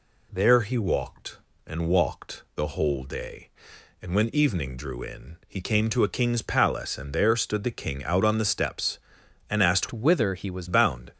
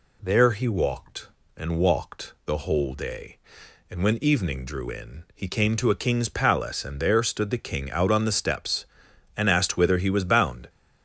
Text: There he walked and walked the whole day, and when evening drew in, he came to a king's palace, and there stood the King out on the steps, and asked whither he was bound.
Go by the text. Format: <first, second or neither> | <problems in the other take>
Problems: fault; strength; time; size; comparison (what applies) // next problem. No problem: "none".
second | changes voice from "whither" to "was"; from 9.9 to 10.6 s; 0.7 s long